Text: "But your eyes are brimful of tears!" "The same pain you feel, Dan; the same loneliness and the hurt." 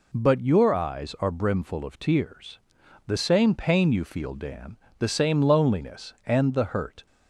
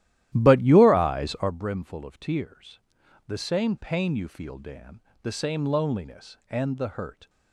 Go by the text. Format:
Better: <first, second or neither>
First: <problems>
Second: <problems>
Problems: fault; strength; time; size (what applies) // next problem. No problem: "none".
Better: first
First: none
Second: starts louder than the rest; strong; until 1.6 s; 13 dB